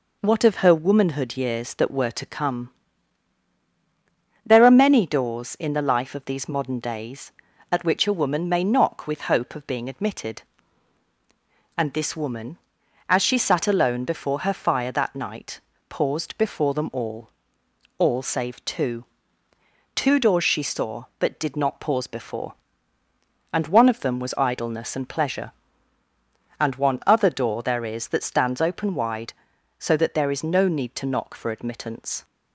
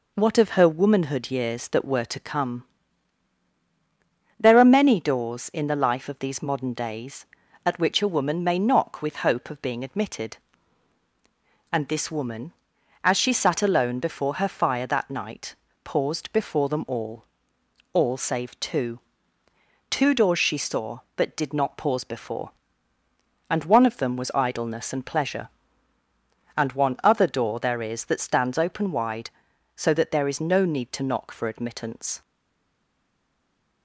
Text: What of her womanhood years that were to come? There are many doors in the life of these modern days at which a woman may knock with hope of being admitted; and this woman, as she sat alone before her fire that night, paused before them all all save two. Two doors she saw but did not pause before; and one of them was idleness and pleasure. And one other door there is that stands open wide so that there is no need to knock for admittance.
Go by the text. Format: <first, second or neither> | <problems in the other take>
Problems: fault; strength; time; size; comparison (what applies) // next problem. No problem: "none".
first | pauses between "all" and "all"; noticeable; at 17.2 s; 0.70 s long; noticeable in the first // stays silent after the last word; noticeable; from 32.2 s on; 1.6 s long